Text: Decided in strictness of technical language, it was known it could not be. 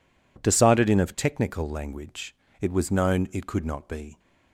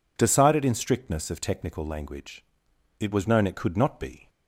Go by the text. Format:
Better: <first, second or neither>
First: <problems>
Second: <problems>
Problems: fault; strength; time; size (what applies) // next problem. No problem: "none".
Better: second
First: skips "strictness"; at 0.9 s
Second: none